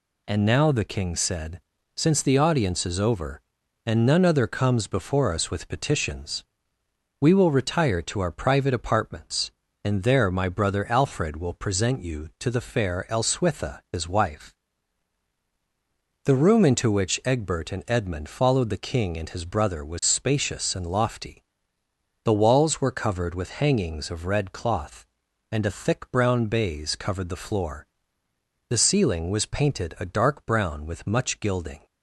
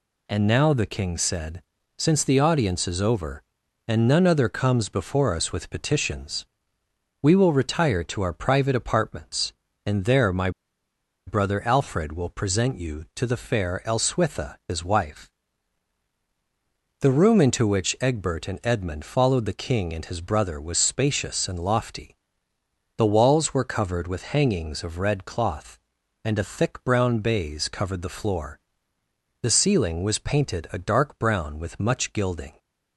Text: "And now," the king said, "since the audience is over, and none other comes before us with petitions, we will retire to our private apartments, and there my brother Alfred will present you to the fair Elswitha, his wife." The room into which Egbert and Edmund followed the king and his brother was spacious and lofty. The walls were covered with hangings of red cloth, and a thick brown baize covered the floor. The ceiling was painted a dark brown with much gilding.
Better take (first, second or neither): first